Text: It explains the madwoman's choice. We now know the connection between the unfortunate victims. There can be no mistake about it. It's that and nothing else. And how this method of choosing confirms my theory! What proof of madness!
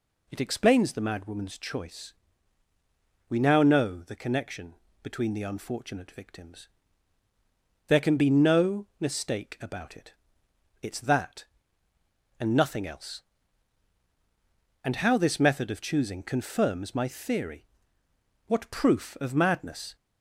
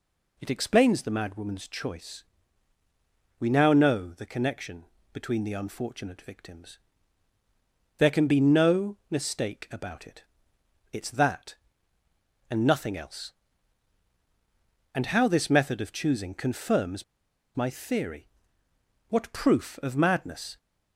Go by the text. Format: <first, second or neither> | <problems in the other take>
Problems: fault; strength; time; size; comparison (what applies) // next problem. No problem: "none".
first | pauses between "connection" and "between"; slight; at 4.8 s; 0.28 s long; slight in the first // pauses between "confirms" and "my"; noticeable; at 17.0 s; 0.53 s long